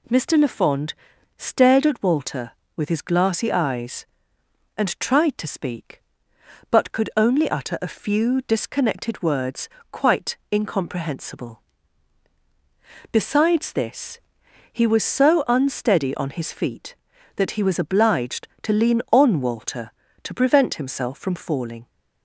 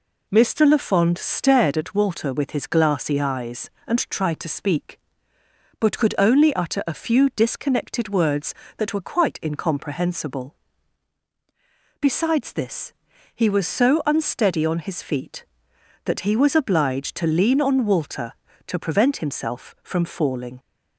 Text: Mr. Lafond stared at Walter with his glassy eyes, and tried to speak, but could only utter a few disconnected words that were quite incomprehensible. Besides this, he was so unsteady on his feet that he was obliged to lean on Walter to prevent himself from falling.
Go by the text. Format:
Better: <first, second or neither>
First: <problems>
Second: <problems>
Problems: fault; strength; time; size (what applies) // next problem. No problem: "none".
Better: second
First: pauses between "Lafond" and "stared"; at 0.9 s; 0.42 s long // skips "that were"; at 9.7 s // pauses between "quite" and "incomprehensible"; slight; at 10.3 s; 0.16 s long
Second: none